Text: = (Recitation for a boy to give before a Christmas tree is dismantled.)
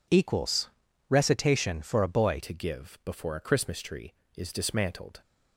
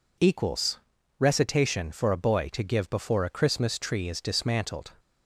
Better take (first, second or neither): second